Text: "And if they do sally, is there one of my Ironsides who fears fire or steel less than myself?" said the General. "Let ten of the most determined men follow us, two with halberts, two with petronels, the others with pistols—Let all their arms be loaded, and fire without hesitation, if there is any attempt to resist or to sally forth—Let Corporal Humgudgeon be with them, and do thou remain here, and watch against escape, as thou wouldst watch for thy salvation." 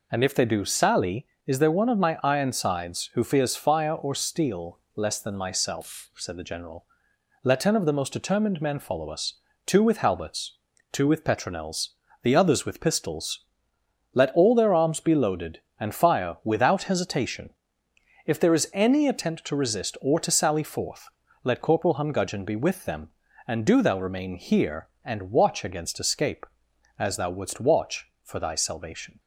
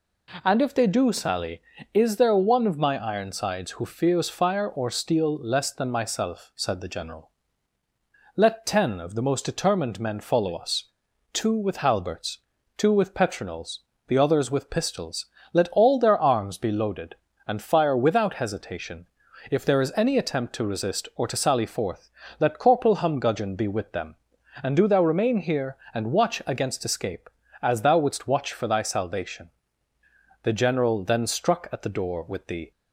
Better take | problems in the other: first | goes on to say "The General then struck at the door with the"; strong; from 30.4 s on; 2.2 s long

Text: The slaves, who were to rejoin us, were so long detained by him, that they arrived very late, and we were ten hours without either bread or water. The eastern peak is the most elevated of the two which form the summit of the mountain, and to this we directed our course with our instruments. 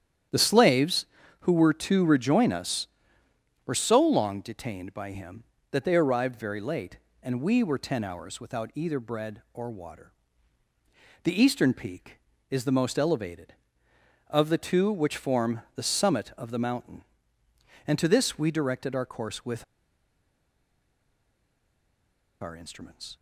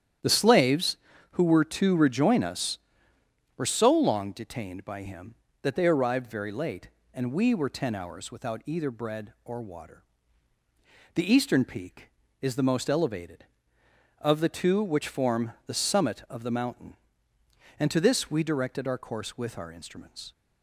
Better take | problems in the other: second | starts louder than the rest; strong; until 1.6 s; 10 dB; strong in the second // pauses between "with" and "our"; strong; at 19.6 s; 2.7 s long

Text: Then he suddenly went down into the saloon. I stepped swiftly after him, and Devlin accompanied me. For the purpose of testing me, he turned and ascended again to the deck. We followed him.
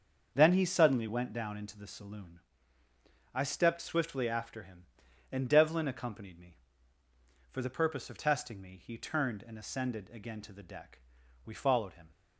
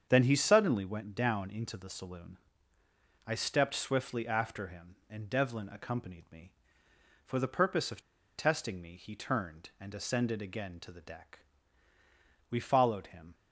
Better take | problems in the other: first | starts louder than the rest; strong; until 1.1 s; 7.5 dB; also in the first // pauses between "of" and "testing"; slight; at 8.0 s; 0.35 s long

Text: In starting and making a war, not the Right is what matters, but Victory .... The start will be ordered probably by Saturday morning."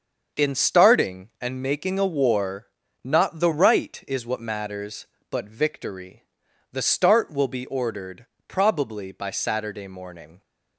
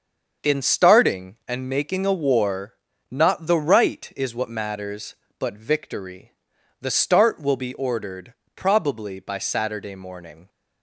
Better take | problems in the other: neither | starts louder than the rest; the same in both // pauses between "ordered" and "probably"; slight; the same in both

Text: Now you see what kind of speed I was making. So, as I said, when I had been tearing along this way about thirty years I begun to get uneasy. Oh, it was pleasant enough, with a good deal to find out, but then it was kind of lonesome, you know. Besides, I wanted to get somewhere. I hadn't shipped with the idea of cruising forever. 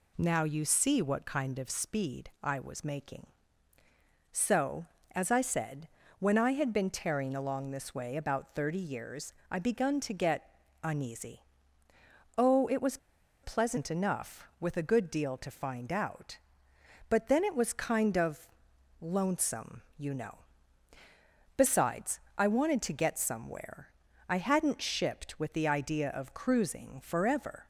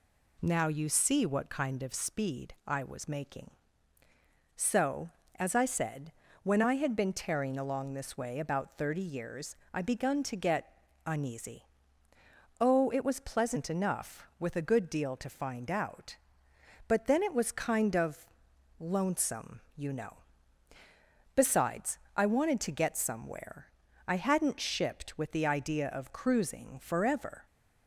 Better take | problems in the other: second | pauses between "years" and "I"; slight; at 9.3 s; 0.16 s long; slight in the second // pauses between "get" and "uneasy"; slight; at 10.4 s; 0.34 s long; slight in the second // pauses between "was" and "pleasant"; at 12.9 s; 0.45 s long // pauses between "of" and "lonesome"; noticeable; at 18.4 s; 0.52 s long; noticeable in the second

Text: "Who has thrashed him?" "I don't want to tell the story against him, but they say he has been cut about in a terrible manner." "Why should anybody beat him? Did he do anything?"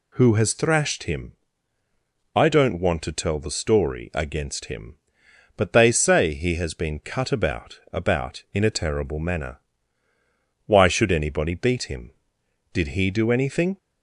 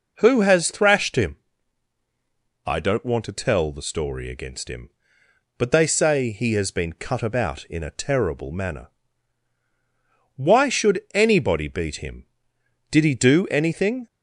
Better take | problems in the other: second | says "about" twice; at 7.9 s

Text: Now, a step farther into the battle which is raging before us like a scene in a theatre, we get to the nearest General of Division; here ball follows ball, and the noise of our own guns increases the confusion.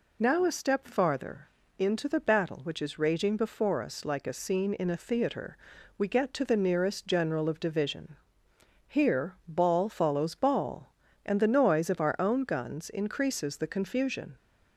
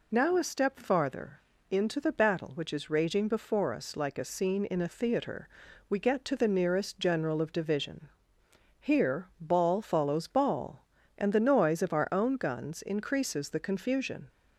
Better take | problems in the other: neither | pauses between "farther" and "into"; slight; the same in both

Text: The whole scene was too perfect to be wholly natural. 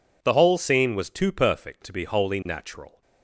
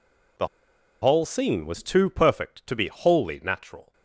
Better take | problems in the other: first | pauses between "The" and "whole"; noticeable; at 0.4 s; 0.55 s long

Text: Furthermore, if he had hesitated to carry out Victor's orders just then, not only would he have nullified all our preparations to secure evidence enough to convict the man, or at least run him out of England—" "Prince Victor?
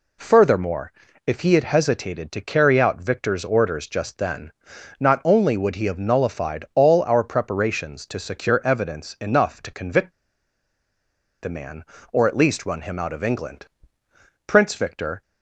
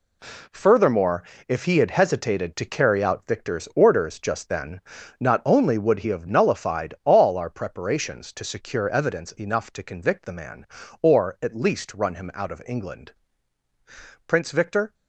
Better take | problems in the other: second | pauses between "convict" and "the"; strong; at 10.1 s; 1.3 s long

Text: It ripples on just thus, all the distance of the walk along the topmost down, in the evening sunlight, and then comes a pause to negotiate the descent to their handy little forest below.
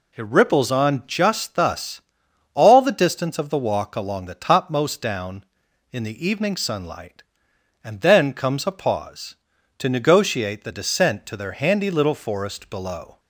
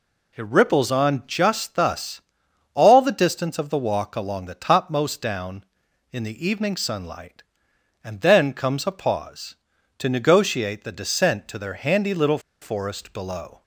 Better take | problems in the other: first | pauses between "little" and "forest"; slight; at 12.3 s; 0.22 s long

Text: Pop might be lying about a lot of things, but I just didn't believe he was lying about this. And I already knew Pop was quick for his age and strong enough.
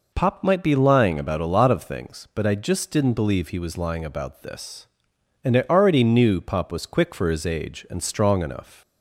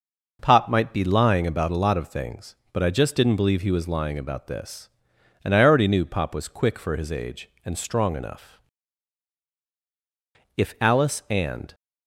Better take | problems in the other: first | goes on to say "If Alice and"; noticeable; from 10.5 s on; 1.1 s long

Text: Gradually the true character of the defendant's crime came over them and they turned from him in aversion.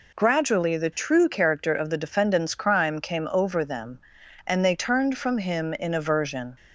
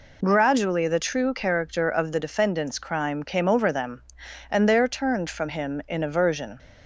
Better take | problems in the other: first | says "there" for "they"; at 4.6 s

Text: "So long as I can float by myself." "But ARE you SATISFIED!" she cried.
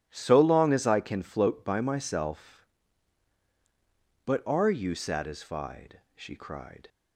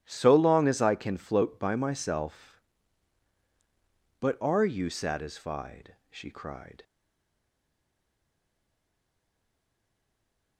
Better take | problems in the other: first | starts louder than the rest; strong; until 1.0 s; 13.5 dB; strong in the first // stays silent after the last word; strong; from 6.8 s on; 3.7 s long

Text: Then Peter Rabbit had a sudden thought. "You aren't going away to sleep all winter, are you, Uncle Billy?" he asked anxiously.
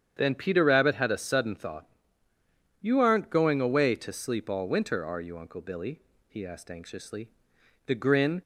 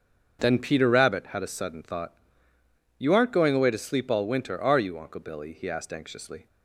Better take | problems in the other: second | starts louder than the rest; strong; until 1.1 s; 8.5 dB; also in the second // goes on to say "The grin"; from 7.8 s on; 0.56 s long

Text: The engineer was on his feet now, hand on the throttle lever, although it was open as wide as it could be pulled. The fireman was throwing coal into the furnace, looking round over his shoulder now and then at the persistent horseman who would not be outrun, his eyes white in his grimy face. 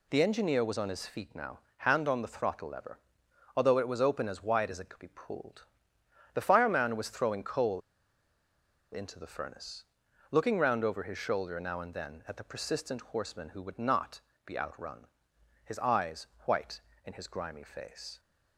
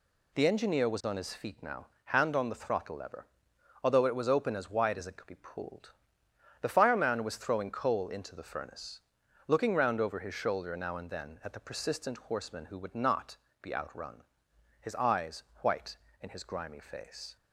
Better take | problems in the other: second | pauses between "coal" and "into"; at 7.8 s; 1.1 s long // pauses between "not" and "be"; slight; at 14.1 s; 0.26 s long; slight in the second // pauses between "eyes" and "white"; slight; at 16.2 s; 0.18 s long; slight in the second

